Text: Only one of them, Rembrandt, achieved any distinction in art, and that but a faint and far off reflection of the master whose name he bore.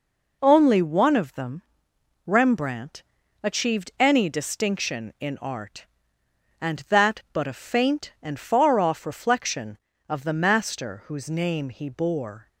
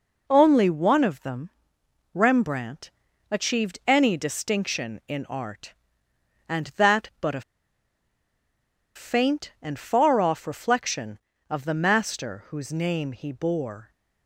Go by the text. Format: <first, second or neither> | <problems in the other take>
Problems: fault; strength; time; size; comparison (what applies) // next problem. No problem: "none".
first | pauses between "a" and "faint"; strong; at 7.4 s; 1.5 s long